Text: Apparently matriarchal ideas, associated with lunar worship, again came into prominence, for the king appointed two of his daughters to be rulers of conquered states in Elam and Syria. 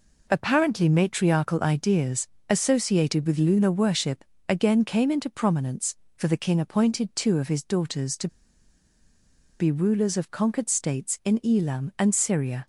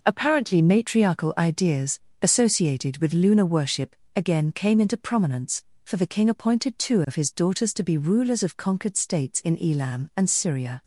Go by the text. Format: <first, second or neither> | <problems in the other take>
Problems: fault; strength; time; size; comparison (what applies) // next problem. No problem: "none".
second | pauses between "to" and "be"; strong; at 8.2 s; 1.3 s long